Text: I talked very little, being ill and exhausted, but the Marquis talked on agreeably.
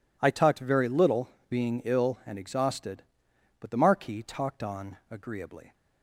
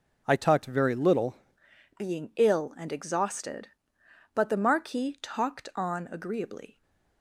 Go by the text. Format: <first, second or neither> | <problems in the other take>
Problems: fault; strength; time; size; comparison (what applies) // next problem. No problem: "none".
first | changes voice at "being"; from 1.9 s on; 4.9 s long // stays silent after the last word; slight; from 6.7 s on; 0.5 s long